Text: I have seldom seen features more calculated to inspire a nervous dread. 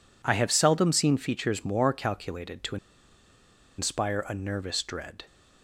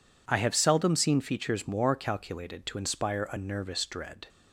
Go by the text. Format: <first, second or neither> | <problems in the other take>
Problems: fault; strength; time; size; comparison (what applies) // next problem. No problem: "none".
second | pauses between "to" and "inspire"; at 2.7 s; 1.0 s long